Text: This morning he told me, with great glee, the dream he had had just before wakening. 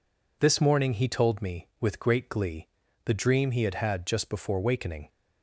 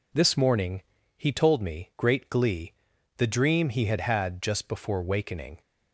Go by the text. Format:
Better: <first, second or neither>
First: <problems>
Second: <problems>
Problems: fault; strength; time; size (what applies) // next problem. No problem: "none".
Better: first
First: none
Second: pauses between "morning" and "he"; slight; at 0.8 s; 0.34 s long // skips "with"; at 1.9 s